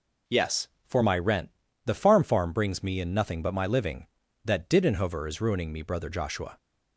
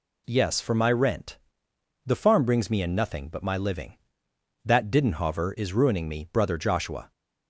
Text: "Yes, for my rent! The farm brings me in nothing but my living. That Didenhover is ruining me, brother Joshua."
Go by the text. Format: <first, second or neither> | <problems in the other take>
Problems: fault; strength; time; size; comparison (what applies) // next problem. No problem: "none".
second | says "farm" twice; at 2.2 s